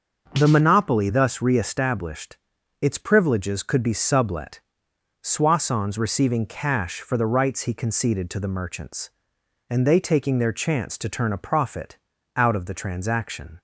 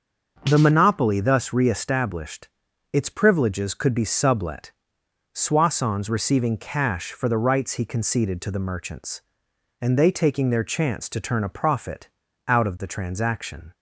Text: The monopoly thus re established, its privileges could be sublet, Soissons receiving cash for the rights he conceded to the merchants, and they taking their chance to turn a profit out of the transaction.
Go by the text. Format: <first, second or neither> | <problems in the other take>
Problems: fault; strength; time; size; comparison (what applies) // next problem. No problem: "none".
neither | starts louder than the rest; the same in both // pauses between "profit" and "out"; the same in both